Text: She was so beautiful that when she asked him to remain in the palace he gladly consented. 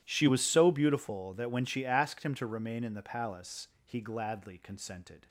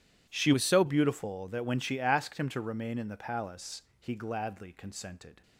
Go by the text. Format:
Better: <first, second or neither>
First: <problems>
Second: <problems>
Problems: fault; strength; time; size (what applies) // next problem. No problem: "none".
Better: first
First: pauses between "palace" and "he"; slight; at 3.6 s; 0.18 s long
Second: changes voice from "was" to "so"; from 0.5 to 0.8 s; 0.3 s long // pauses between "palace" and "he"; slight; at 3.8 s; 0.18 s long